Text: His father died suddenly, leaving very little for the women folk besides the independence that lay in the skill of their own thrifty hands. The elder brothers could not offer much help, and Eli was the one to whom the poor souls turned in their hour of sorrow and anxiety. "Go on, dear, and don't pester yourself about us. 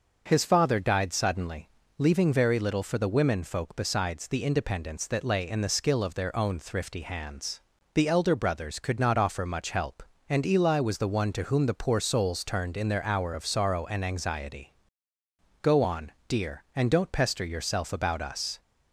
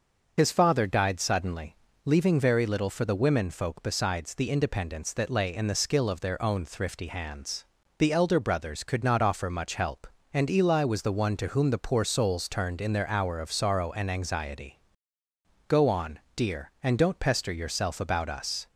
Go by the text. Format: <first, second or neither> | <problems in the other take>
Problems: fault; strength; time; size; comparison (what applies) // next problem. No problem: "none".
first | loses the start of "His"; at 0.3 s; 55 ms // starts louder than the rest; until 1.3 s; 6.5 dB; also in the first